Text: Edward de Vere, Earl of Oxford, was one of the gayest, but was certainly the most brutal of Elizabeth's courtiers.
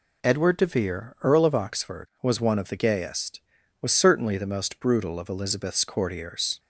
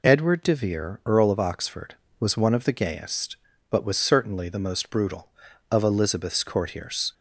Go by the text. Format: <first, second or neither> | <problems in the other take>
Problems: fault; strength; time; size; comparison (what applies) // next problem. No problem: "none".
second | skips "but"; at 3.6 s